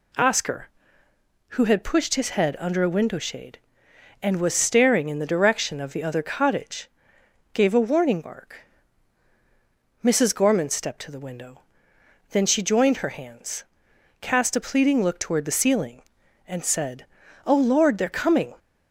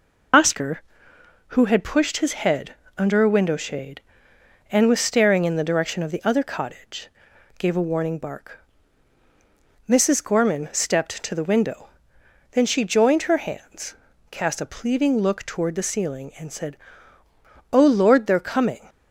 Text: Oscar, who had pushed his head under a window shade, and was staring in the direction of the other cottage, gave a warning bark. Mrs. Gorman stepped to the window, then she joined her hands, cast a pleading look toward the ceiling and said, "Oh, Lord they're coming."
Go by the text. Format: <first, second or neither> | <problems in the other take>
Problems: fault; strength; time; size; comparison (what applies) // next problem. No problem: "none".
first | loses the start of "Oscar"; at 0.3 s; 75 ms // pauses between "head" and "under"; slight; at 2.7 s; 0.22 s long